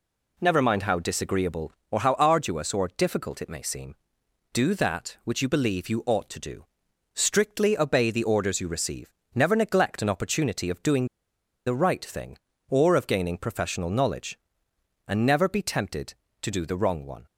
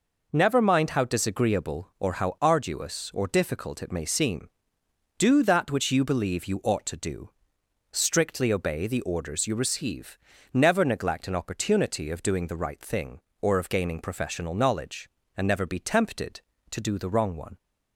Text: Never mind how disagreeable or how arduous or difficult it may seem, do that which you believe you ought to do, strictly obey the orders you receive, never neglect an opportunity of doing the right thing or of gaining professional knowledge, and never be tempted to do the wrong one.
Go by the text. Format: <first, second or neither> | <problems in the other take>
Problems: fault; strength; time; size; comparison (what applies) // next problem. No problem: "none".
second | pauses between "doing" and "the"; noticeable; at 11.0 s; 0.59 s long